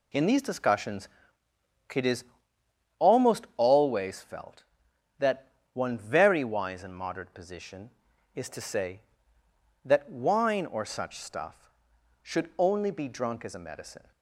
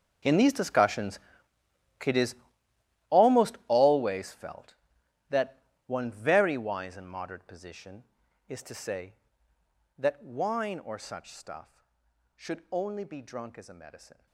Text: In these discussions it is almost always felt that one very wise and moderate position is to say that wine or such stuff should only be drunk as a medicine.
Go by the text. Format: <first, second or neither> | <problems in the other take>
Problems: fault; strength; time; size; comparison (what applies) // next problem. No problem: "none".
first | gets quieter; strong; throughout; 17.5 dB // pauses between "discussions" and "it"; noticeable; at 1.1 s; 0.86 s long; noticeable in the first // pauses between "is" and "almost"; noticeable; at 2.3 s; 0.74 s long; noticeable in the first // pauses between "that" and "one"; slight; at 5.5 s; 0.28 s long; slight in the first